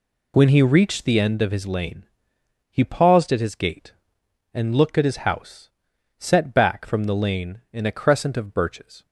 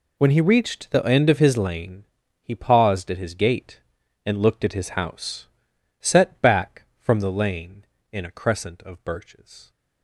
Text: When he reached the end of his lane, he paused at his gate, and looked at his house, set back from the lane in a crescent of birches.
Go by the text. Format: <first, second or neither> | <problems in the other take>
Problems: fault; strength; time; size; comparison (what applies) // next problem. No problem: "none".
neither | none